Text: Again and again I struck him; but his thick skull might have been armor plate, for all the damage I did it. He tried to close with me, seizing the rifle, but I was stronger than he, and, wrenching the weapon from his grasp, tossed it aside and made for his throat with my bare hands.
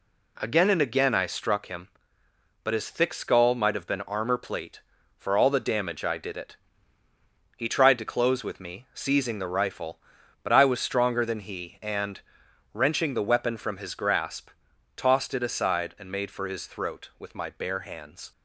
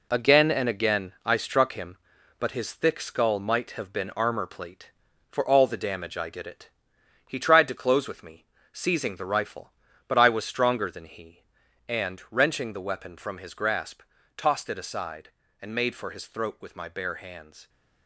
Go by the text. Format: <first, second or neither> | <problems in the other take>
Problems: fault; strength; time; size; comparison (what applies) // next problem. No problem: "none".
first | gets quieter; strong; throughout; 8 dB